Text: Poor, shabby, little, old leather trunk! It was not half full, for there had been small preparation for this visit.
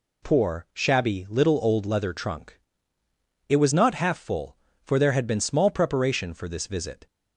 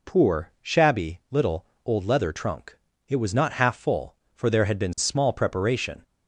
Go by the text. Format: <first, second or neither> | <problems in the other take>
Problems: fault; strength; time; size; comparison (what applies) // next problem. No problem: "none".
first | stops before "for this visit"; at 6.0 s